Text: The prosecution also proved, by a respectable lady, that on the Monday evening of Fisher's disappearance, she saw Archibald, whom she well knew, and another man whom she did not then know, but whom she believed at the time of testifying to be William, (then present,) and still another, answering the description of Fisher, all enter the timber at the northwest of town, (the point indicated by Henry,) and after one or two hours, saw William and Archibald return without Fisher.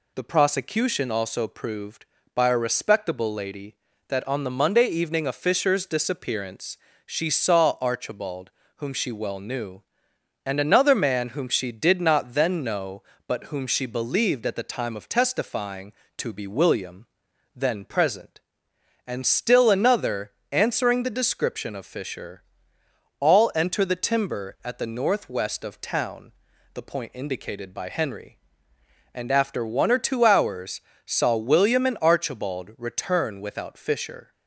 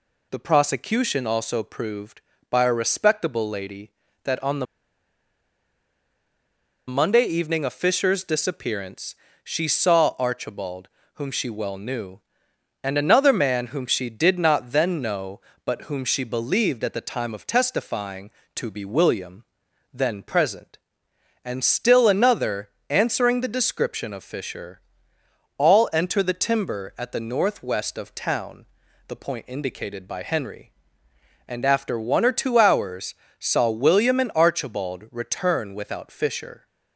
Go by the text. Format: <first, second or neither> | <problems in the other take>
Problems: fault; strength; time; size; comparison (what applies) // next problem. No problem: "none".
first | pauses between "the" and "Monday"; strong; at 4.6 s; 2.2 s long